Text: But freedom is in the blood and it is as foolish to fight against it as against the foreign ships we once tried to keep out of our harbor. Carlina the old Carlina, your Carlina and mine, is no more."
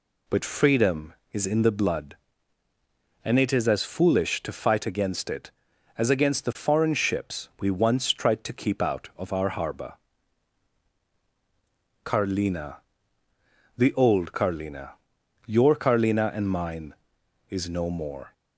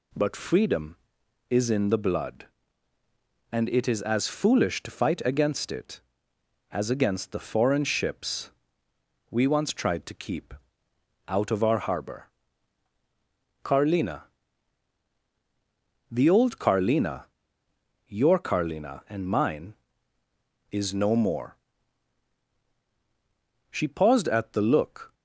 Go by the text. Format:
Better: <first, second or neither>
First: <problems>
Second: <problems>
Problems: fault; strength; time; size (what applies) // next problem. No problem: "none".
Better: first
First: pauses between "Carlina" and "the"; at 12.7 s; 1.0 s long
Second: pauses between "ships" and "we"; noticeable; at 8.5 s; 0.78 s long // pauses between "keep" and "out"; noticeable; at 10.5 s; 0.74 s long // pauses between "Carlina" and "the"; strong; at 14.2 s; 1.9 s long // goes on to say "She paused at the look"; from 23.6 s on; 1.4 s long